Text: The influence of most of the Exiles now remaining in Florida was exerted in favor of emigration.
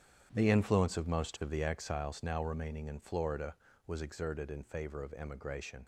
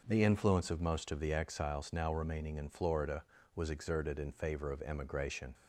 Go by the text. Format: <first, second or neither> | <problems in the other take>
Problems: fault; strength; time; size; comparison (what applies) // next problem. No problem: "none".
second | gets quieter; strong; throughout; 12 dB